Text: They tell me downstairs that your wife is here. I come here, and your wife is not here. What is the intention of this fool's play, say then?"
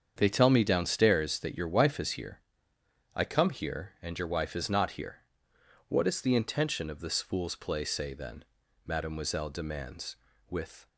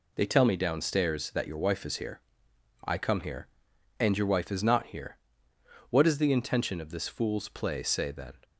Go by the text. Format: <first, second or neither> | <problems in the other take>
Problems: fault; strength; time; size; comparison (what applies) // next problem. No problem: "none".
second | starts louder than the rest; strong; until 1.1 s; 7.5 dB // goes on to say "mademoiselle demands with"; strong; from 8.8 s on; 2.0 s long